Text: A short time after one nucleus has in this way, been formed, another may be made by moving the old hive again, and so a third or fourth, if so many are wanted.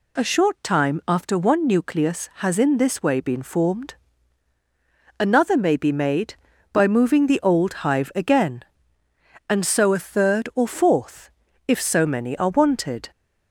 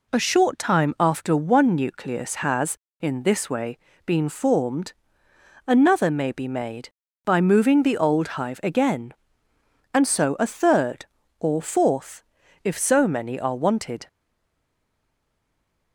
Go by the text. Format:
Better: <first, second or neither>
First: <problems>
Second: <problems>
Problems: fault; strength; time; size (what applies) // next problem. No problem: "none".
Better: first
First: none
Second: stays silent after the last word; noticeable; from 14.0 s on; 1.9 s long